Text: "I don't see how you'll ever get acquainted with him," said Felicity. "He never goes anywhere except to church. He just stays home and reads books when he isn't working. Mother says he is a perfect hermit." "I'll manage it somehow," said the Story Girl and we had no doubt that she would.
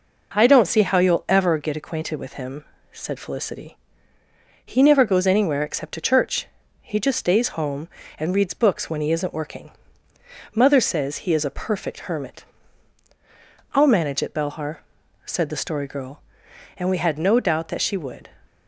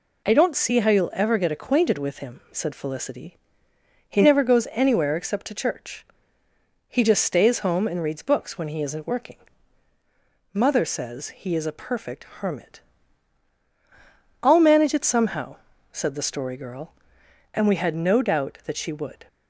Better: second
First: says "belhar" for "somehow"; at 14.3 s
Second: none

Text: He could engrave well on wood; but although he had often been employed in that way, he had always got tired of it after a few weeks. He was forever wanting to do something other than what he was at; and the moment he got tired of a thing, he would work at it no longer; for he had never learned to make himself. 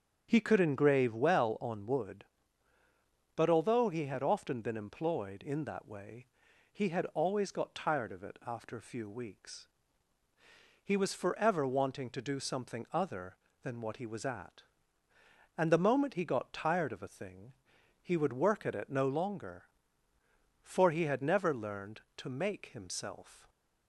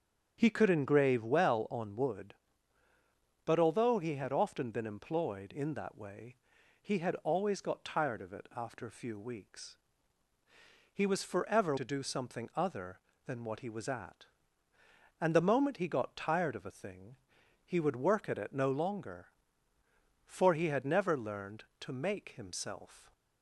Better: first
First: starts louder than the rest; strong; until 1.3 s; 8 dB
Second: starts louder than the rest; strong; until 1.3 s; 7.5 dB // skips "wanting"; at 11.7 s

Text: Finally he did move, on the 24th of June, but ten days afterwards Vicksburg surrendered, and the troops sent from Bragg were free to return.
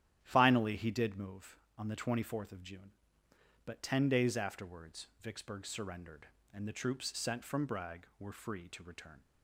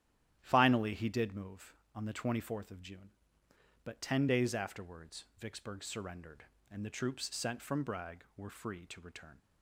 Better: neither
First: starts louder than the rest; strong; until 1.2 s; 11.5 dB // pauses between "afterwards" and "Vicksburg"; slight; at 5.0 s; 0.16 s long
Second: starts louder than the rest; strong; until 1.4 s; 11.5 dB // pauses between "afterwards" and "Vicksburg"; slight; at 5.2 s; 0.16 s long

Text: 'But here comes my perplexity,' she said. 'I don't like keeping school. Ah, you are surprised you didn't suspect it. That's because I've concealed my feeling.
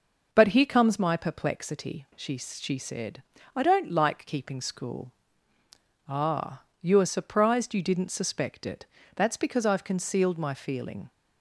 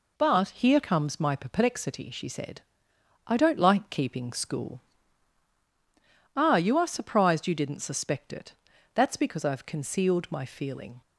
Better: second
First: says "she" twice; at 2.3 s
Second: none

